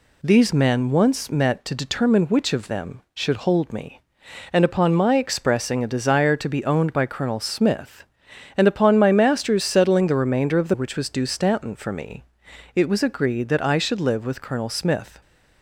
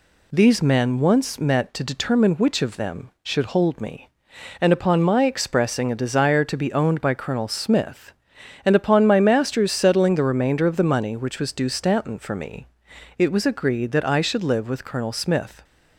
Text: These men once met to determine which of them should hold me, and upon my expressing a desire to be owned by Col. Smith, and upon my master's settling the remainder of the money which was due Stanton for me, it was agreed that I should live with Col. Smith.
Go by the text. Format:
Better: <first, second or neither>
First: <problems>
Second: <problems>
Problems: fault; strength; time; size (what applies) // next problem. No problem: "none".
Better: second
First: skips "money"; at 10.7 s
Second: none